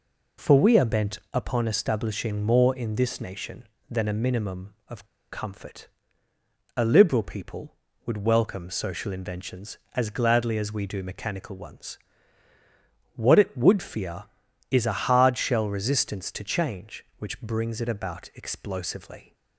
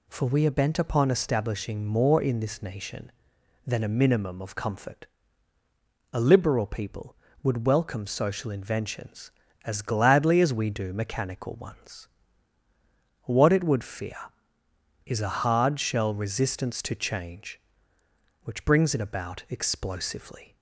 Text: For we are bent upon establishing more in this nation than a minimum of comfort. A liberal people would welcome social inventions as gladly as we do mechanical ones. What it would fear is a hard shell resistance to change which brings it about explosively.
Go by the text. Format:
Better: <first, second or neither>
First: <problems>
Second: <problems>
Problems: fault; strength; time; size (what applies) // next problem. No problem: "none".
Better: second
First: pauses between "bent" and "upon"; slight; at 1.1 s; 0.16 s long // pauses between "of" and "comfort"; slight; at 5.0 s; 0.26 s long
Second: none